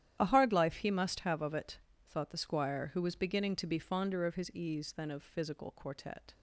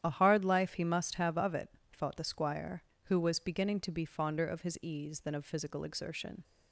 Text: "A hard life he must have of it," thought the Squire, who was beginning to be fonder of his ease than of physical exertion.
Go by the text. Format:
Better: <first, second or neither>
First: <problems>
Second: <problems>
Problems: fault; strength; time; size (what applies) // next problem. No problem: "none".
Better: second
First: starts louder than the rest; strong; until 1.2 s; 11 dB // says "quartet" for "exertion"; at 5.7 s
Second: starts louder than the rest; strong; until 1.0 s; 10.5 dB